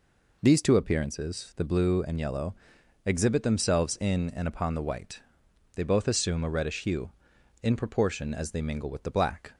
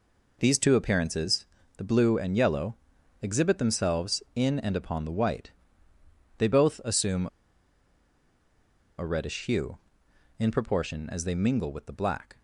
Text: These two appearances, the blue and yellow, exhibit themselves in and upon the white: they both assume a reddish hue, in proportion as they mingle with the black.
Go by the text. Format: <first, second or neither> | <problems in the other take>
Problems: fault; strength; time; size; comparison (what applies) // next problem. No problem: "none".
first | pauses between "assume" and "a"; strong; at 7.2 s; 1.7 s long